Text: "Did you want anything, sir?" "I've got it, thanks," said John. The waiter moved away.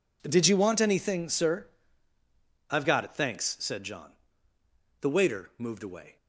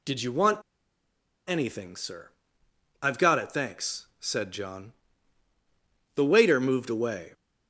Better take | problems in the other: first | pauses between "want" and "anything"; noticeable; at 0.6 s; 0.87 s long

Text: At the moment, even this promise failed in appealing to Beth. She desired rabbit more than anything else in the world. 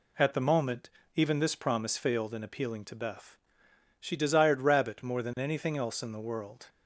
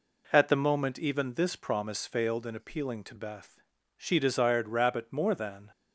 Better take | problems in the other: first | stops before "anything else in the world"; at 5.7 s

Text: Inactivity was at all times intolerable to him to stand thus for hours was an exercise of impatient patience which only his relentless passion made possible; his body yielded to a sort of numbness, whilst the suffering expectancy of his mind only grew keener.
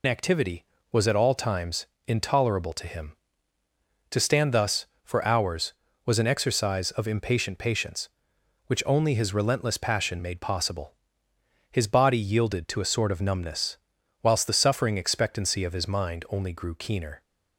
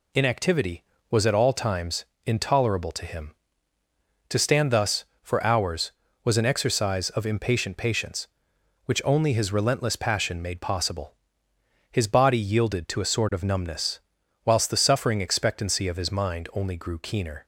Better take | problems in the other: second | loses the start of "Inactivity"; at 0.0 s; 80 ms // pauses between "times" and "intolerable"; slight; at 1.8 s; 0.20 s long; slight in the second

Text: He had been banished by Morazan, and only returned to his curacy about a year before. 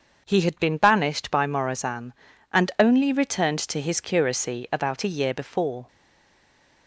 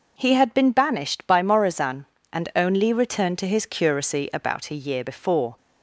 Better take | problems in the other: second | starts louder than the rest; until 1.2 s; 6 dB // stays silent after the last word; from 5.8 s on; 1.0 s long

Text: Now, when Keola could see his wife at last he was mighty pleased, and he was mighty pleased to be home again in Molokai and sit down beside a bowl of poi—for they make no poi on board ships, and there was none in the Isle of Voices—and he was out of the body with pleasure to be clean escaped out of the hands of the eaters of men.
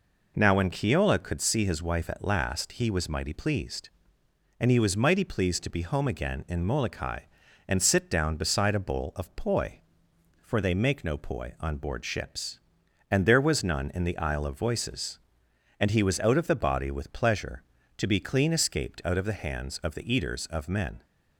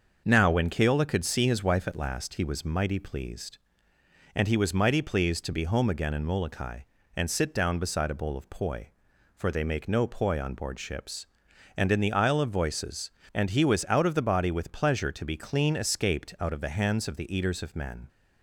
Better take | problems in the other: first | starts louder than the rest; until 1.2 s; 6.5 dB // skips "there was none"; at 11.9 s

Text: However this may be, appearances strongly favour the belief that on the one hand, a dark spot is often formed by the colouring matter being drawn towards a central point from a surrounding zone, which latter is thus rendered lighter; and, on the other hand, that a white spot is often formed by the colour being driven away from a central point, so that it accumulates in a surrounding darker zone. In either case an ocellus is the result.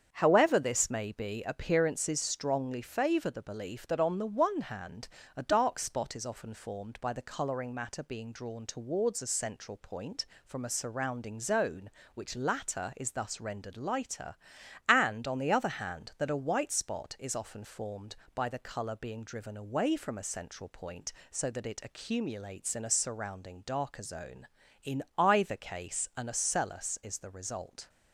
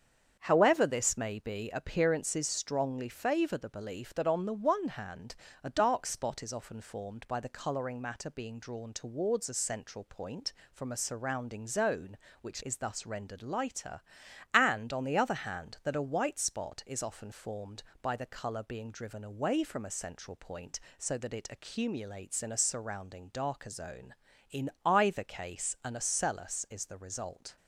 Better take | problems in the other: first | starts louder than the rest; strong; until 1.4 s; 7.5 dB; strong in the first // skips "latter"; at 12.6 s // pauses between "In" and "either"; slight; at 24.6 s; 0.16 s long; slight in the first

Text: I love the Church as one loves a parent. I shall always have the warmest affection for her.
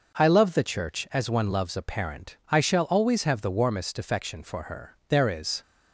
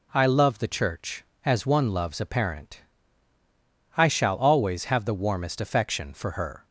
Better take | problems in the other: second | goes on to say "There is"; from 5.0 s on; 0.52 s long

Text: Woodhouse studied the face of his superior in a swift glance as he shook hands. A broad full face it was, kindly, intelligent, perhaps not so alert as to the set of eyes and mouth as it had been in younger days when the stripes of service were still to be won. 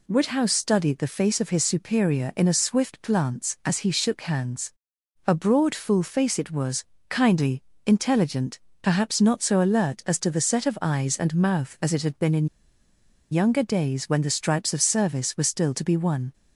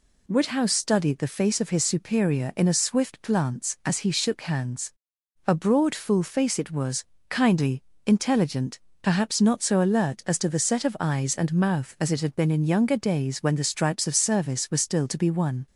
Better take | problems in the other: second | pauses between "in" and "younger"; noticeable; at 12.4 s; 0.85 s long

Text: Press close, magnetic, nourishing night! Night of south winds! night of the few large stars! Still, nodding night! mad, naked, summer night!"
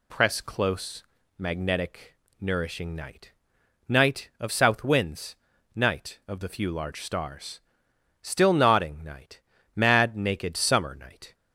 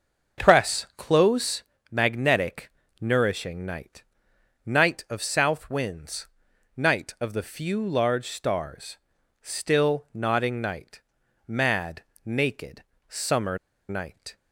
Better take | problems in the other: first | starts louder than the rest; noticeable; until 1.4 s; 6 dB // pauses between "summer" and "night"; slight; at 13.5 s; 0.31 s long

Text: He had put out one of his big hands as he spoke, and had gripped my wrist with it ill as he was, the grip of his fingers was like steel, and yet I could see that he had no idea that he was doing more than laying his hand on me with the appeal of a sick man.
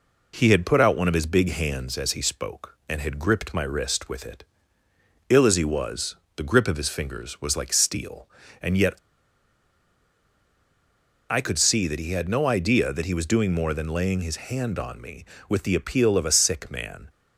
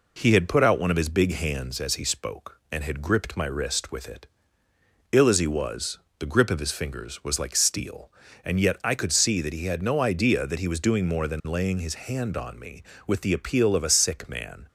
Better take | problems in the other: second | pauses between "it" and "ill"; noticeable; at 4.4 s; 0.86 s long; noticeable in the second // pauses between "yet" and "I"; strong; at 8.9 s; 2.3 s long

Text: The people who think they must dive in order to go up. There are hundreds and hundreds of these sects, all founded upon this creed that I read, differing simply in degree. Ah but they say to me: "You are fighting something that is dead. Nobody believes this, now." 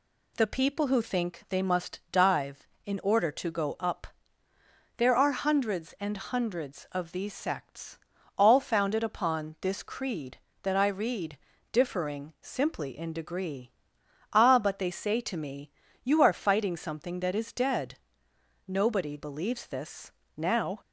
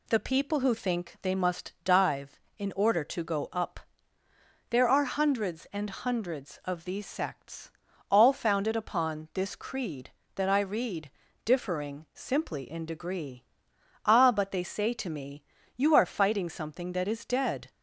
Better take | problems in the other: first | stops before "Nobody believes this now"; at 17.6 s

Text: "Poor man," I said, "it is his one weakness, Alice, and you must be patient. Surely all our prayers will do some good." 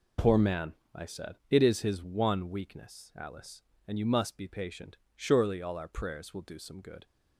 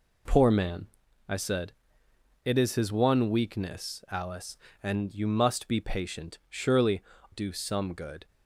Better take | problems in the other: first | skips "all our prayers will"; at 7.1 s

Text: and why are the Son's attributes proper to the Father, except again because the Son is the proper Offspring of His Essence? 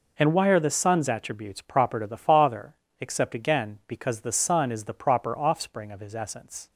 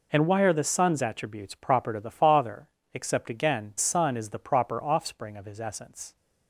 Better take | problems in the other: first | skips "because the"; at 3.7 s

